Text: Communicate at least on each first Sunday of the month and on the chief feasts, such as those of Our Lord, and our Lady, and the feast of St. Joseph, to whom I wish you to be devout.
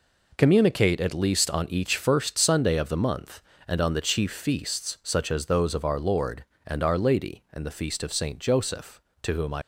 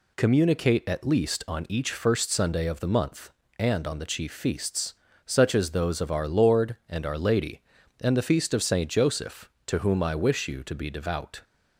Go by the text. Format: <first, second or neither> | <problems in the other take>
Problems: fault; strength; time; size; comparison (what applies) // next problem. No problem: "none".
second | stops before "wish you to be devout"; at 9.6 s